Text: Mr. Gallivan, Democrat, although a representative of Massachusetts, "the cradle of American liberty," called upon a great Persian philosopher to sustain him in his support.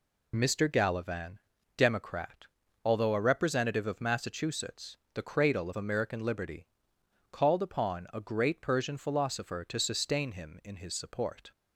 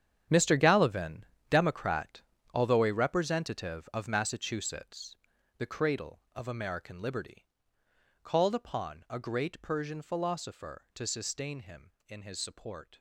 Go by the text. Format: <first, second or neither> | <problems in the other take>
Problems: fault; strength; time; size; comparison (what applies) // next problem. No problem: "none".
first | gets quieter; strong; throughout; 14.5 dB